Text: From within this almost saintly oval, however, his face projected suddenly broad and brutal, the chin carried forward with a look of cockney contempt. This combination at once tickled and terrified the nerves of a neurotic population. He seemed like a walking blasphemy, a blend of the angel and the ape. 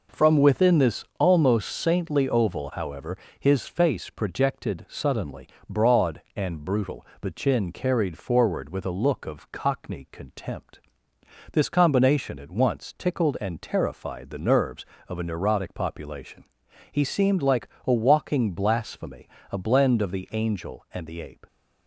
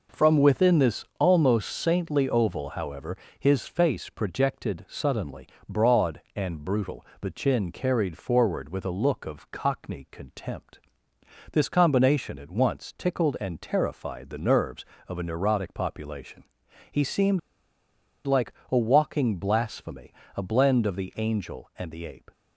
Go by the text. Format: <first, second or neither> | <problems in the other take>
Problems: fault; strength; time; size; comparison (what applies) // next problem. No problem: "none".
first | pauses between "suddenly" and "broad"; slight; at 5.4 s; 0.22 s long; slight in the first // pauses between "seemed" and "like"; noticeable; at 17.3 s; 0.85 s long // pauses between "like" and "a"; slight; at 18.5 s; 0.16 s long; slight in the first